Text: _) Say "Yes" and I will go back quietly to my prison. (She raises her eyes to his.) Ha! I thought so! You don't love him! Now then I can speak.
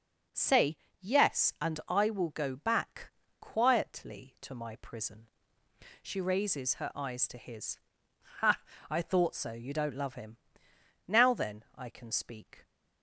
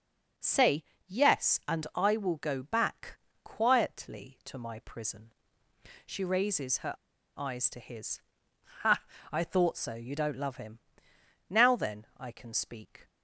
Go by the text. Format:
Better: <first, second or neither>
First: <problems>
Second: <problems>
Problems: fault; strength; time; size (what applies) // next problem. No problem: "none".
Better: first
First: pauses between "Say" and "Yes"; slight; at 0.7 s; 0.24 s long // pauses between "back" and "quietly"; slight; at 3.1 s; 0.29 s long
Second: pauses between "Say" and "Yes"; slight; at 0.8 s; 0.24 s long // pauses between "back" and "quietly"; slight; at 3.1 s; 0.26 s long // pauses between "her" and "eyes"; at 6.9 s; 0.44 s long